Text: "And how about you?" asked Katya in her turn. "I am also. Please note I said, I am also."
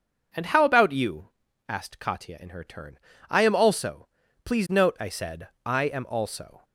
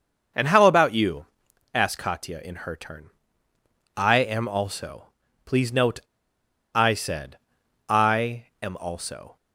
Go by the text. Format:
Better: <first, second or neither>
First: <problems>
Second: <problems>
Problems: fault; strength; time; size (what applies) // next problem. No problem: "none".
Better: first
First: none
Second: starts louder than the rest; until 1.8 s; 6.5 dB // pauses between "note" and "I"; noticeable; at 5.9 s; 0.74 s long // pauses between "I" and "am"; slight; at 8.4 s; 0.18 s long